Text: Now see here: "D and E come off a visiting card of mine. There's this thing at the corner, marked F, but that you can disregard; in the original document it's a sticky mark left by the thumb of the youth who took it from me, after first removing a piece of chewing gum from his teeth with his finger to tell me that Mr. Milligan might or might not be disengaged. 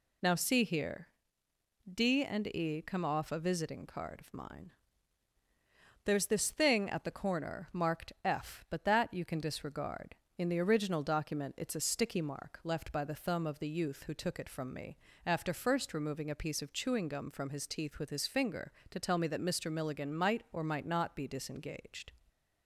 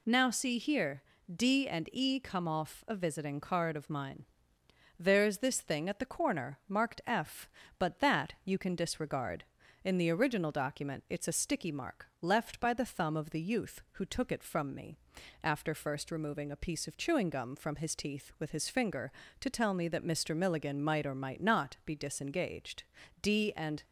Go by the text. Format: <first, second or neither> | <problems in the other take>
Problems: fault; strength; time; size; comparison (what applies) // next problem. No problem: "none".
first | goes on to say "D and"; noticeable; from 23.2 s on; 0.62 s long